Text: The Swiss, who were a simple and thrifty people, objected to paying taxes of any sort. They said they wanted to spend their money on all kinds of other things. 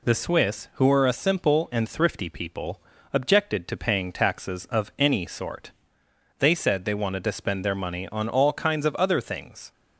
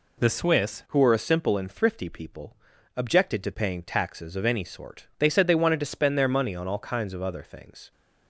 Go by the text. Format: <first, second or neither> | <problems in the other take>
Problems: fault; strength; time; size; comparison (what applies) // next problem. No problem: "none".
first | changes voice at "who"; from 0.8 s on; 7.1 s long